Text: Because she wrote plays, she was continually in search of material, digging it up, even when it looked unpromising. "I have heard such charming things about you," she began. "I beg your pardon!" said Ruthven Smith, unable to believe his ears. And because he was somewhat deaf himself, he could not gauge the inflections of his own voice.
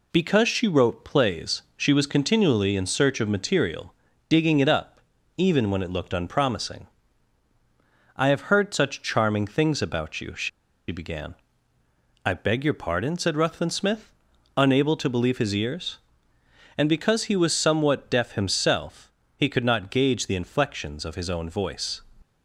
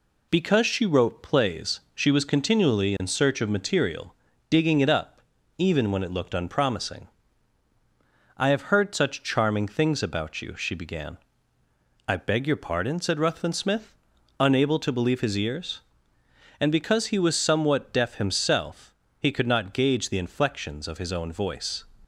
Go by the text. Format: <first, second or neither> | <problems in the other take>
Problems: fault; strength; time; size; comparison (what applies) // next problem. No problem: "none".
second | pauses between "she" and "began"; at 10.4 s; 0.40 s long